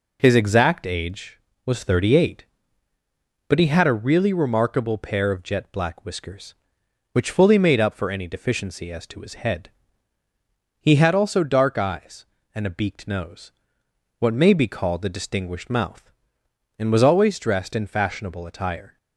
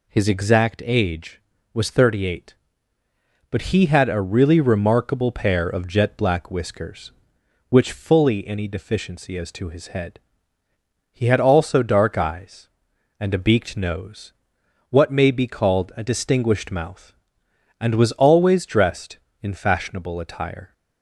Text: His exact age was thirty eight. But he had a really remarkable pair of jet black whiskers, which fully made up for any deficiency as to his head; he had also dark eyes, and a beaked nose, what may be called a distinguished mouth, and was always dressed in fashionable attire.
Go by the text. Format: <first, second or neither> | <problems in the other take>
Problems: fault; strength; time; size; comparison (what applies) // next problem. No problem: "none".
first | skips "made up for"; at 8.4 s